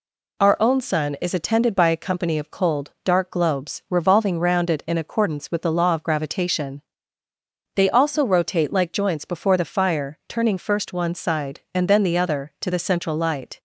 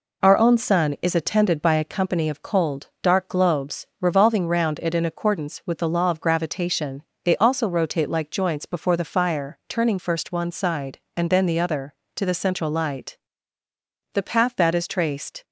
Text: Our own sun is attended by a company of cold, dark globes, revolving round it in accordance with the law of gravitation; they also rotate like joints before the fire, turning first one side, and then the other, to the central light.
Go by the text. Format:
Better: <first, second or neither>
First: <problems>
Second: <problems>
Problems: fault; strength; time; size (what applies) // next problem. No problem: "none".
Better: first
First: none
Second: goes on to say "The path that is traced"; noticeable; from 14.1 s on; 1.3 s long